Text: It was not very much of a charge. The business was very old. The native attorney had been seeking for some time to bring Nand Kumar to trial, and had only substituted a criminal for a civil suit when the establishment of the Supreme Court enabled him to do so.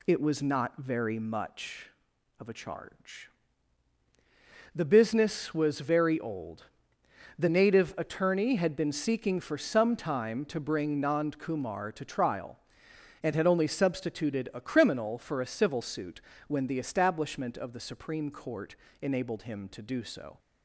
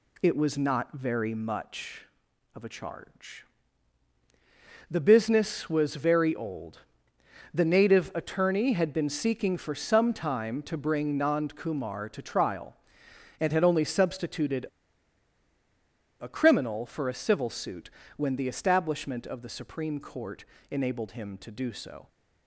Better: first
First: pauses between "suit" and "when"; slight; at 16.2 s; 0.26 s long // pauses between "Court" and "enabled"; slight; at 18.7 s; 0.24 s long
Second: pauses between "substituted" and "a"; strong; at 14.6 s; 1.5 s long // pauses between "suit" and "when"; slight; at 17.8 s; 0.26 s long // pauses between "Court" and "enabled"; slight; at 20.4 s; 0.24 s long

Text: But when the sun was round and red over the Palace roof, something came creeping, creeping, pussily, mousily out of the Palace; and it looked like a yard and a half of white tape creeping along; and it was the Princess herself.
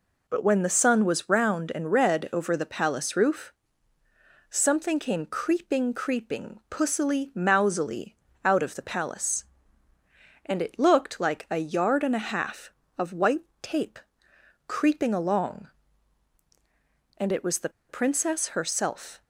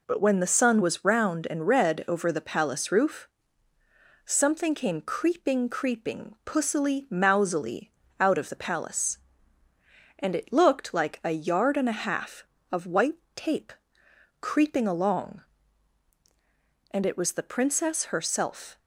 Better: second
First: pauses between "mousily" and "out"; slight; at 8.1 s; 0.28 s long // pauses between "white" and "tape"; slight; at 13.4 s; 0.16 s long // pauses between "tape" and "creeping"; noticeable; at 13.9 s; 0.68 s long // pauses between "the" and "Princess"; slight; at 17.6 s; 0.19 s long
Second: pauses between "mousily" and "out"; slight; at 7.9 s; 0.28 s long // pauses between "white" and "tape"; slight; at 13.1 s; 0.16 s long // pauses between "tape" and "creeping"; noticeable; at 13.7 s; 0.68 s long

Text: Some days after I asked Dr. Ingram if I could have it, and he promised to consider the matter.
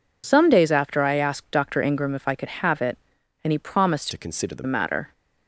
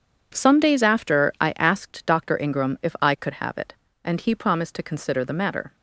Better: second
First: changes voice from "to" to "the"; from 4.1 to 4.6 s; 0.5 s long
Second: none

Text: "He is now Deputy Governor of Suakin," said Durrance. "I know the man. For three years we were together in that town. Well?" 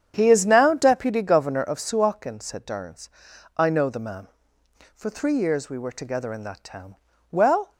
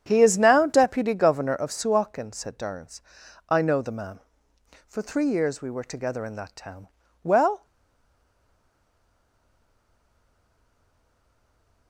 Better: first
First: starts louder than the rest; strong; until 1.1 s; 8.5 dB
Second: starts louder than the rest; strong; until 1.0 s; 8.5 dB // stays silent after the last word; strong; from 7.6 s on; 4.2 s long

